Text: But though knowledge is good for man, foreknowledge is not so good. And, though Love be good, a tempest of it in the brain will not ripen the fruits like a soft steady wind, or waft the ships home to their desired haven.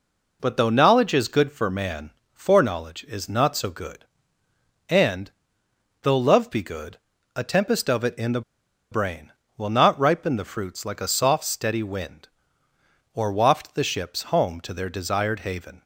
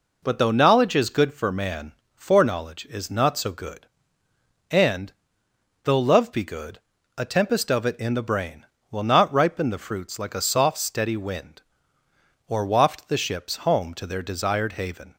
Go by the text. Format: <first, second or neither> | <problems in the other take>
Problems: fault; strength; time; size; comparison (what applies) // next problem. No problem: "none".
second | pauses between "the" and "brain"; noticeable; at 8.4 s; 0.50 s long